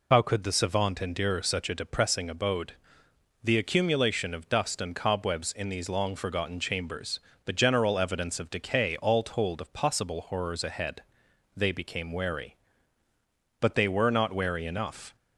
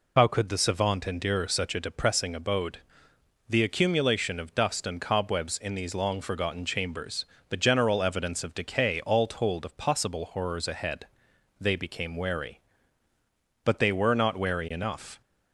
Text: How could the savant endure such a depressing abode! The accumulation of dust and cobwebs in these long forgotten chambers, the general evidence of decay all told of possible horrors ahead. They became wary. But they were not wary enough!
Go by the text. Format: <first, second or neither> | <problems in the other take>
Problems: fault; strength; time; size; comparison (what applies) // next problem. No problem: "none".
neither | none